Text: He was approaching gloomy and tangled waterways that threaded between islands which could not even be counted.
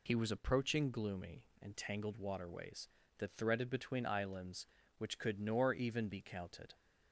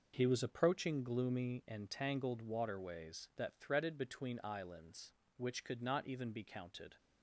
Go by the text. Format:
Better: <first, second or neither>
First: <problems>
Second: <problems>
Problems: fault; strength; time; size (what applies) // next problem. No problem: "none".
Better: second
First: says "nor" for "not"; at 5.4 s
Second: none